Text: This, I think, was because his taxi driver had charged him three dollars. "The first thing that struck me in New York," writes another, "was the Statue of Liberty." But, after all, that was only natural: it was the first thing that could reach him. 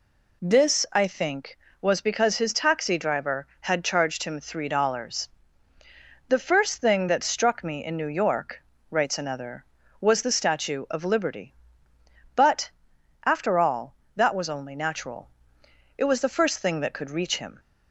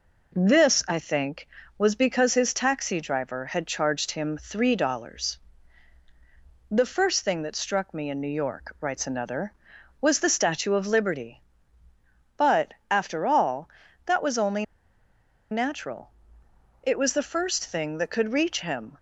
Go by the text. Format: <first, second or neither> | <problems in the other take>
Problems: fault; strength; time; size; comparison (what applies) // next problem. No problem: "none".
first | pauses between "only" and "natural"; noticeable; at 14.6 s; 0.86 s long